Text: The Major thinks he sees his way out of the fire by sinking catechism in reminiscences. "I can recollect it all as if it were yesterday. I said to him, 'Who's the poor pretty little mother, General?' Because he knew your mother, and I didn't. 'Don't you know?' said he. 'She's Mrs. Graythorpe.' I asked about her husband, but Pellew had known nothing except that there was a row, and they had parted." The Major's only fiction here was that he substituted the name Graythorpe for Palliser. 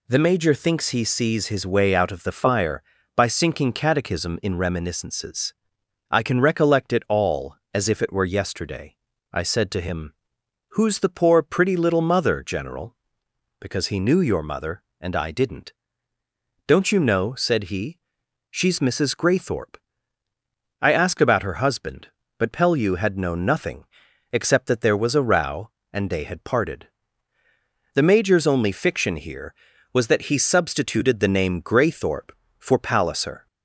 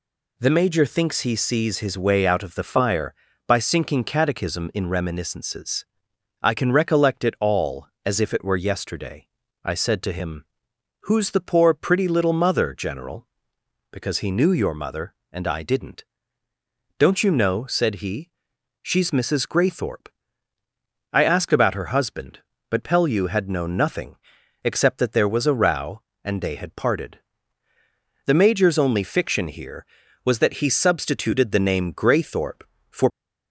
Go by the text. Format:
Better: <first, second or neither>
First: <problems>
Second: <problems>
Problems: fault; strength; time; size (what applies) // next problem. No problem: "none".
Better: first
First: pauses between "nothing" and "except"; noticeable; at 23.8 s; 0.48 s long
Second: pauses between "nothing" and "except"; noticeable; at 24.1 s; 0.48 s long // stops before "Palliser"; at 33.1 s